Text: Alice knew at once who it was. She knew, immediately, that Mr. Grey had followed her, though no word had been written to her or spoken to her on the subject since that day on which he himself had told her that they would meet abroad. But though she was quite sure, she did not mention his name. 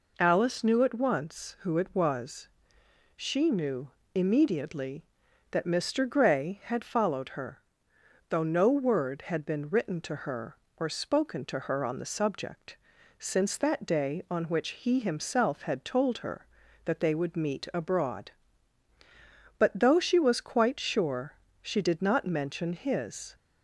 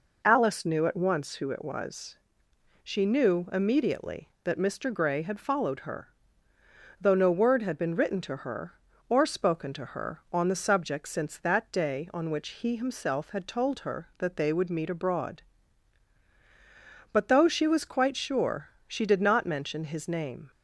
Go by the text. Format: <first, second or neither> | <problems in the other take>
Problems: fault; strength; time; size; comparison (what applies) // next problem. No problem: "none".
second | pauses between "subject" and "since"; at 12.7 s; 0.42 s long // stops before "name"; at 23.3 s